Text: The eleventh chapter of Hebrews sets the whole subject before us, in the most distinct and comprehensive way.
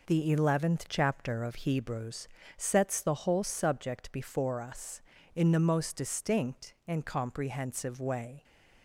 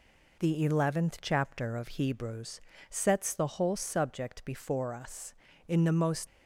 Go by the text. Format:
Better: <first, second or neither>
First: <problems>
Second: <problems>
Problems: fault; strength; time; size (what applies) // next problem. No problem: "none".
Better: first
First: pauses between "Hebrews" and "sets"; slight; at 2.2 s; 0.30 s long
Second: pauses between "Hebrews" and "sets"; slight; at 2.5 s; 0.30 s long // stops before "distinct and comprehensive way"; at 6.2 s